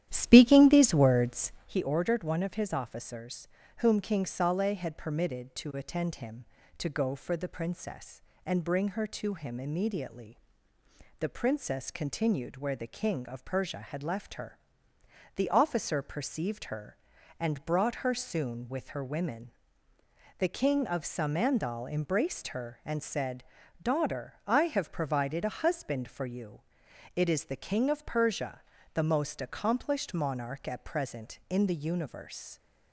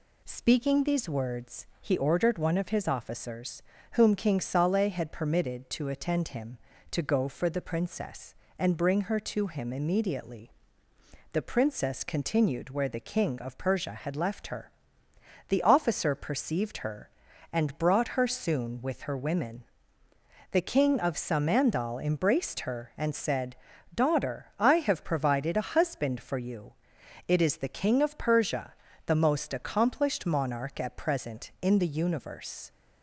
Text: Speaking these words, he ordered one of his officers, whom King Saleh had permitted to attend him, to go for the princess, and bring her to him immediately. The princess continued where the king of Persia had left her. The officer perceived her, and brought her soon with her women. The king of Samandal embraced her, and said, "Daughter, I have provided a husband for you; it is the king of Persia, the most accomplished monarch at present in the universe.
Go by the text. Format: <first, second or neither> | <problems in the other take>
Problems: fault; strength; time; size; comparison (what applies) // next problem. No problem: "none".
second | starts louder than the rest; strong; until 1.7 s; 11.5 dB